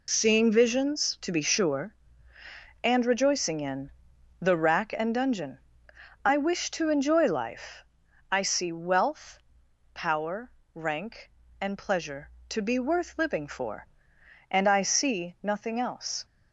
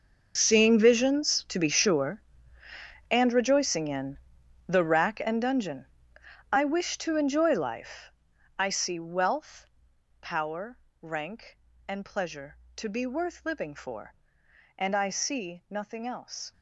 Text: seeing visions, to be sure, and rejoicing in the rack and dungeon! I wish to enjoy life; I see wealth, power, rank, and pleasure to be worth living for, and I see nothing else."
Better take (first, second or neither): first